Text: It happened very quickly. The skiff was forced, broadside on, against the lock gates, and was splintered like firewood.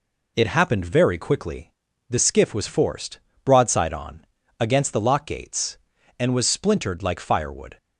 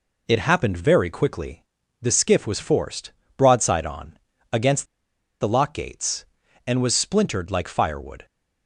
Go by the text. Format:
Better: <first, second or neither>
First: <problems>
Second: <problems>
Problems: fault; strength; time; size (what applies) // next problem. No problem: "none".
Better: first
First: none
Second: pauses between "against" and "the"; noticeable; at 4.8 s; 0.56 s long